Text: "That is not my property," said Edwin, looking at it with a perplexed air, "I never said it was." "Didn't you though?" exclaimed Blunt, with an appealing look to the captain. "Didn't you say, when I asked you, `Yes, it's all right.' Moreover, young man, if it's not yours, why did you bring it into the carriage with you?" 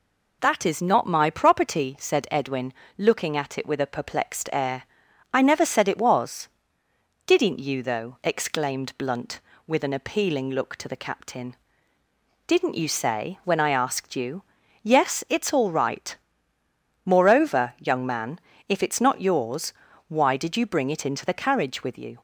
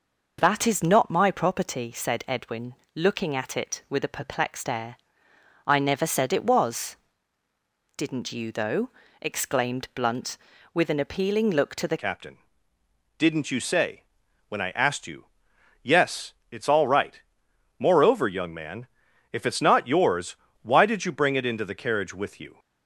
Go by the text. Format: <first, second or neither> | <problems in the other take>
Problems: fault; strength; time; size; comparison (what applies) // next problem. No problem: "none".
first | changes voice at "captain"; from 11.9 s on; 10.6 s long